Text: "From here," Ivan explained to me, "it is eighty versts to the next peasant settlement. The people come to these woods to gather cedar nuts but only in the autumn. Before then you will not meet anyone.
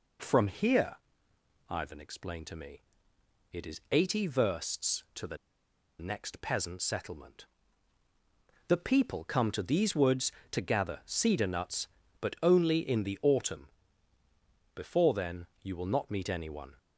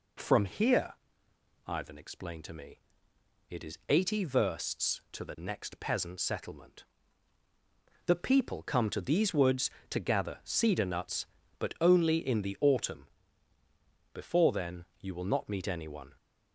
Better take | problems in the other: second | pauses between "the" and "next"; noticeable; at 5.3 s; 0.63 s long // pauses between "then" and "you"; slight; at 15.4 s; 0.16 s long; slight in the second

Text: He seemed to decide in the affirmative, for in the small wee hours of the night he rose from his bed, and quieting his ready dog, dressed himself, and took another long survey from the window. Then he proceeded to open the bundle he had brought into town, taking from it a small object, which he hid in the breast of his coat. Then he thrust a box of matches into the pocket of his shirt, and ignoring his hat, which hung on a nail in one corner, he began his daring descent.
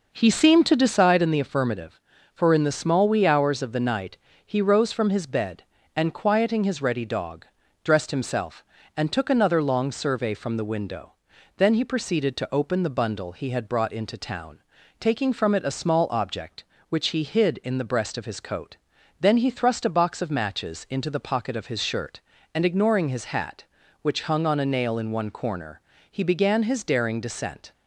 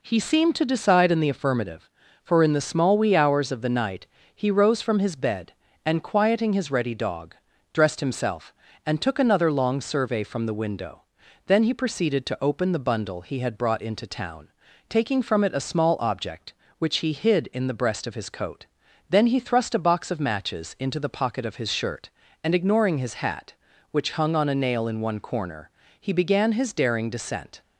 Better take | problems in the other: second | starts louder than the rest; noticeable; until 1.0 s; 5.5 dB // pauses between "night" and "he"; slight; at 4.1 s; 0.28 s long; slight in the second

